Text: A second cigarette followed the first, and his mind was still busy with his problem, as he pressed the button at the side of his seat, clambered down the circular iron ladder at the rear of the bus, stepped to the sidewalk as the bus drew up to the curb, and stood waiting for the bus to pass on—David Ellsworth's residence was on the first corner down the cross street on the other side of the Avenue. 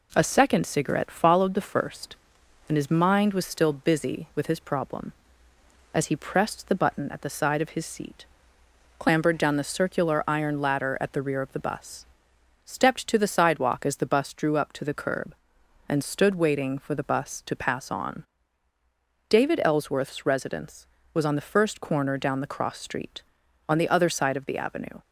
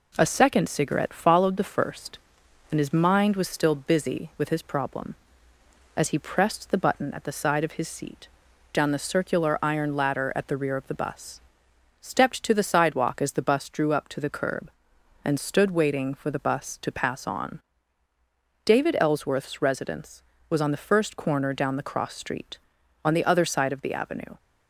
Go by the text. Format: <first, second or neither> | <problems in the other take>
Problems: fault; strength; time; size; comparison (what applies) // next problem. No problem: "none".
first | skips "clambered"; at 8.5 s